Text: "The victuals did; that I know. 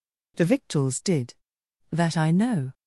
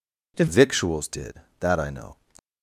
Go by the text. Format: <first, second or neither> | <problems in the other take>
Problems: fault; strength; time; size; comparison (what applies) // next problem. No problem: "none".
first | changes voice at "victuals"; from 0.4 s on; 1.7 s long